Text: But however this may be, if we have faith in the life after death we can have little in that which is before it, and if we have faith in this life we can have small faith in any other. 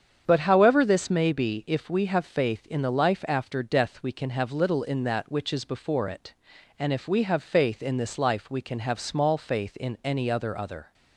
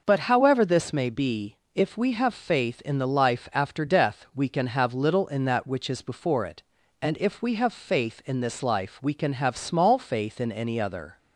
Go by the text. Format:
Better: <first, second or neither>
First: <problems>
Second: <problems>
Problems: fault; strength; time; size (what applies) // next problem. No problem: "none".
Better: second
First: starts louder than the rest; strong; until 1.2 s; 8 dB // says "other" twice; at 10.5 s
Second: none